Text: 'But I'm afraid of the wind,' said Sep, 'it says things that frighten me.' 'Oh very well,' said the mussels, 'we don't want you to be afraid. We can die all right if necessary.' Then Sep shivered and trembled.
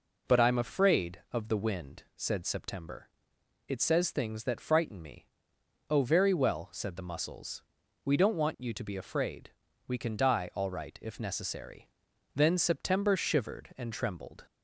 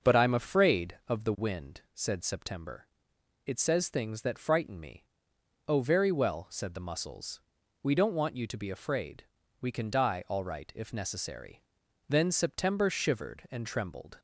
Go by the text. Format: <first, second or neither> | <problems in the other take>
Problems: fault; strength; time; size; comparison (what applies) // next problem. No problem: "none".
first | starts louder than the rest; until 1.4 s; 6.5 dB